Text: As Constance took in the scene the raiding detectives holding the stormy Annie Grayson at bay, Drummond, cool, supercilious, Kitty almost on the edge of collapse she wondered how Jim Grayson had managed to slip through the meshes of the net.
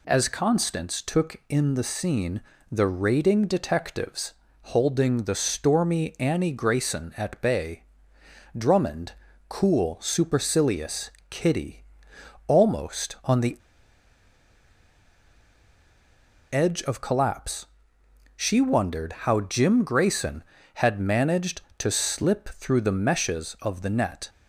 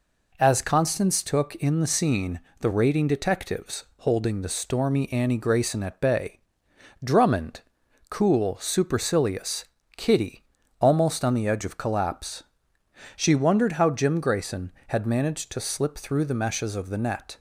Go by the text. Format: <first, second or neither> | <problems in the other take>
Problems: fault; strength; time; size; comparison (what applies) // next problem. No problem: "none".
second | pauses between "scene" and "the"; slight; at 2.4 s; 0.30 s long; slight in the second // pauses between "detectives" and "holding"; slight; at 4.3 s; 0.26 s long // pauses between "Kitty" and "almost"; noticeable; at 11.8 s; 0.64 s long; slight in the second // pauses between "the" and "edge"; strong; at 13.5 s; 2.9 s long // pauses between "collapse" and "she"; noticeable; at 17.6 s; 0.72 s long; noticeable in the second